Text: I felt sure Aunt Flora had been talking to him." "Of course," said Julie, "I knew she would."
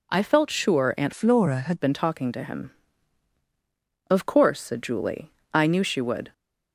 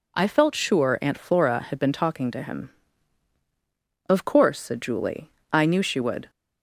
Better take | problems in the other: second | changes voice from "Flora" to "had"; from 1.1 to 1.8 s; 0.7 s long

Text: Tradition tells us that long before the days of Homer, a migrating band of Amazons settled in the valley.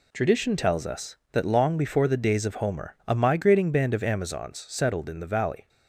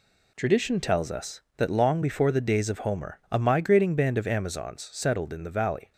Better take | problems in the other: neither | none

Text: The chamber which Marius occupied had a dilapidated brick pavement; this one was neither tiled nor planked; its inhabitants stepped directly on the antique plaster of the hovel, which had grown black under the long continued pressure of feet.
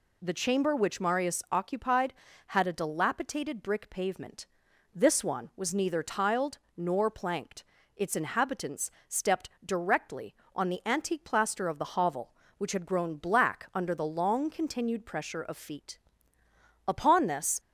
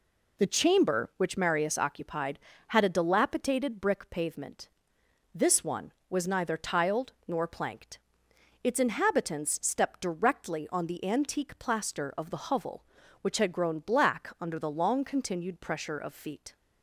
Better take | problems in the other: second | pauses between "tiled" and "nor"; slight; at 6.5 s; 0.20 s long; slight in the second // pauses between "inhabitants" and "stepped"; slight; at 8.8 s; 0.20 s long // goes on to say "Upon this"; noticeable; from 16.8 s on; 0.72 s long

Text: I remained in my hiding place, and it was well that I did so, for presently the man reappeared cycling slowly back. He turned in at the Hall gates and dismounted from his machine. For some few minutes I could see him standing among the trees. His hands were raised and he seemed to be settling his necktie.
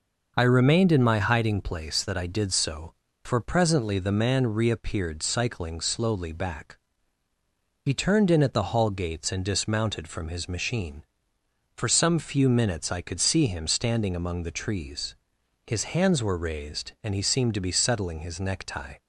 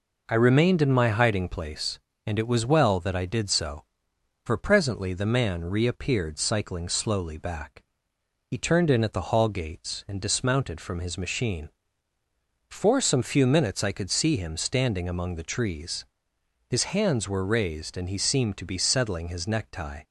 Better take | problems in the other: second | skips "and it was well"; at 2.0 s

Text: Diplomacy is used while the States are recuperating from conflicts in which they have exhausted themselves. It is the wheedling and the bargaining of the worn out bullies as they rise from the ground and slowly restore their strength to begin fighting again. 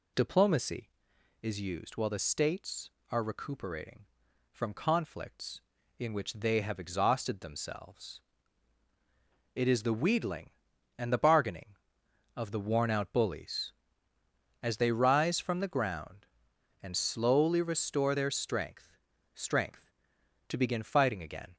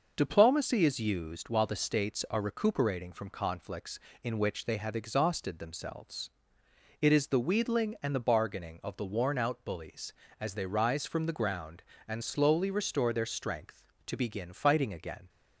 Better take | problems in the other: second | says "strength" twice; at 19.3 s

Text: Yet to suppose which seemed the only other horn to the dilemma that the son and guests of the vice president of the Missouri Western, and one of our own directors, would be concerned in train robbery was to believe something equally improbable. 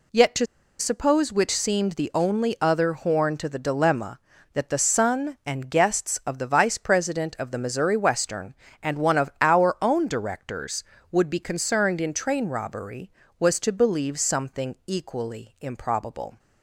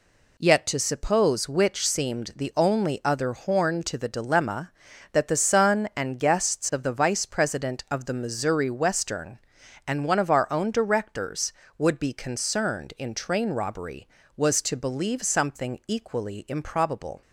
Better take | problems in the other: second | pauses between "to" and "suppose"; slight; at 0.4 s; 0.34 s long

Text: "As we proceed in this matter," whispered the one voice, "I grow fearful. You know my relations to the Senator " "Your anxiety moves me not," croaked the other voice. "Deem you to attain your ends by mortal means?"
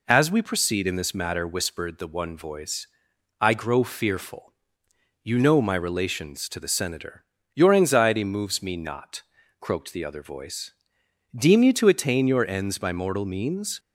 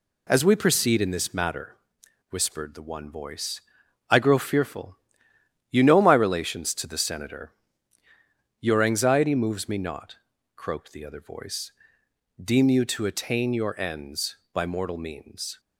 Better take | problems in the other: neither | none

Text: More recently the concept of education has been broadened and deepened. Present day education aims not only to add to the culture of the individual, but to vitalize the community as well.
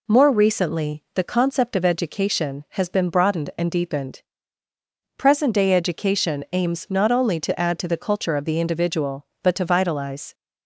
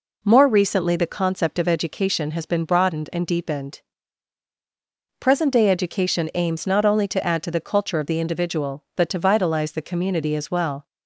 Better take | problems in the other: second | stops before "the community as well"; at 10.3 s

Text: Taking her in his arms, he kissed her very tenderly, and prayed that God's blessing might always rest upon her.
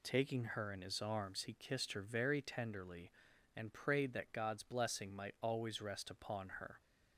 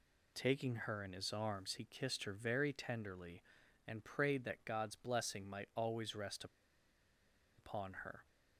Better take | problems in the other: first | pauses between "rest" and "upon"; at 6.4 s; 1.1 s long

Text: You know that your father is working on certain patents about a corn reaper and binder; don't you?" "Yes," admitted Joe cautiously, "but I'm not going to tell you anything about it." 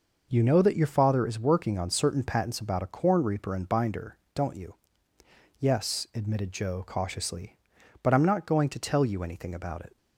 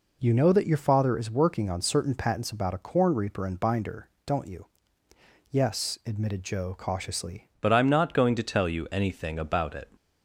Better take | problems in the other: first | changes voice at "but"; from 7.6 s on; 2.3 s long

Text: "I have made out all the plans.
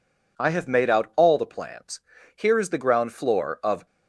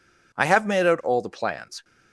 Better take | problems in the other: second | goes on to say "Here is the ground floor of"; from 2.3 s on; 1.5 s long

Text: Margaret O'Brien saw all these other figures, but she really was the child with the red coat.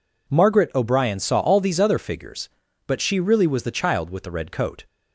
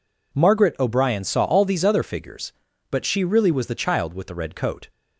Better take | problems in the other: neither | none

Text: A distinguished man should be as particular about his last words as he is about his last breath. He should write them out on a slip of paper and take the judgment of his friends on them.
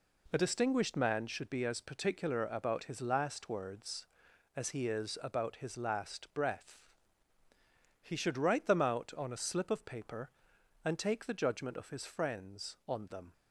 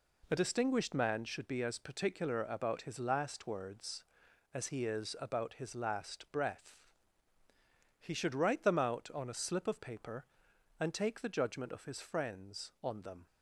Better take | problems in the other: neither | none

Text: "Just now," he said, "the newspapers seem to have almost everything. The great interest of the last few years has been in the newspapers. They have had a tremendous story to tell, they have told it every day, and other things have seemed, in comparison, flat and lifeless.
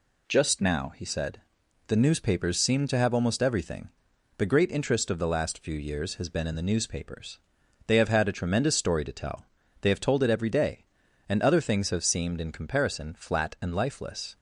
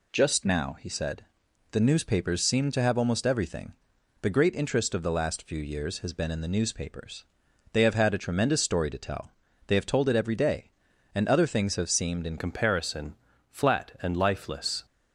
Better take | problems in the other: first | changes voice at "comparison"; from 12.3 s on; 2.5 s long

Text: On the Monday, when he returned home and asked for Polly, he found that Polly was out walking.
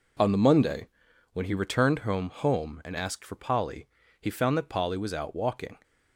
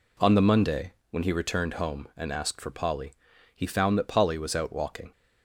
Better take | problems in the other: second | says "home" twice; at 2.2 s

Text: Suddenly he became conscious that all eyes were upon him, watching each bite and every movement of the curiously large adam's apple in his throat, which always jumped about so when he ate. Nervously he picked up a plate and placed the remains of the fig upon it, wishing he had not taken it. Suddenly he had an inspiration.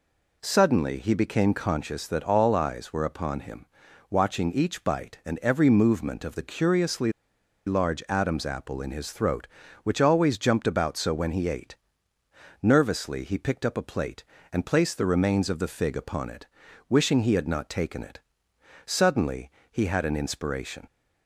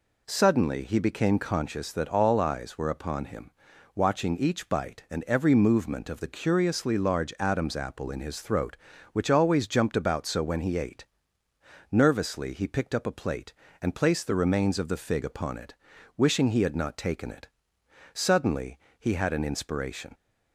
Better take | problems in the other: second | pauses between "curiously" and "large"; noticeable; at 7.1 s; 0.54 s long // pauses between "Suddenly" and "he"; slight; at 19.4 s; 0.22 s long; slight in the second

